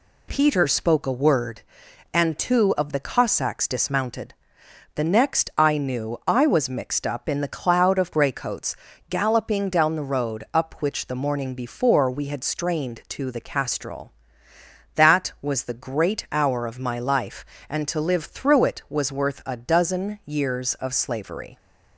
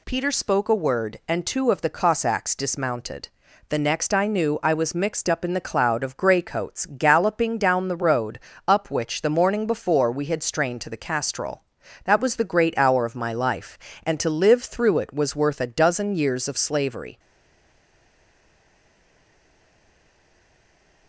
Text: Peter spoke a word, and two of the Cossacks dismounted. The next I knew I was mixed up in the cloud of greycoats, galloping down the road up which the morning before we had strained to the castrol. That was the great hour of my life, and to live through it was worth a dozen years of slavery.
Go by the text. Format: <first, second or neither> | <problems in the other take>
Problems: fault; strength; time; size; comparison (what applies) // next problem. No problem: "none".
first | pauses between "road" and "up"; slight; at 8.3 s; 0.29 s long // stays silent after the last word; strong; from 17.1 s on; 3.9 s long